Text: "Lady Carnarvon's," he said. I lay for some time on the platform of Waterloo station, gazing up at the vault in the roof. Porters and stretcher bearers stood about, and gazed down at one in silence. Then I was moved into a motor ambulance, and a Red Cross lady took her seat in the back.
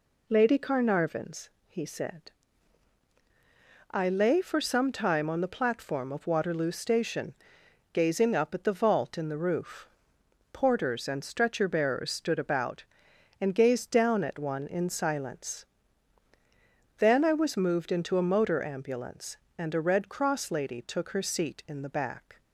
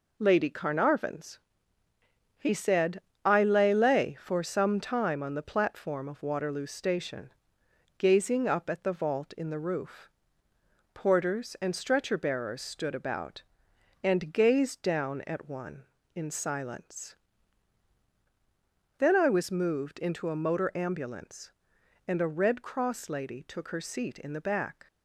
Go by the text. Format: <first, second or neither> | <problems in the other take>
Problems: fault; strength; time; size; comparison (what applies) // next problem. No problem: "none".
first | says "lay" twice; at 3.7 s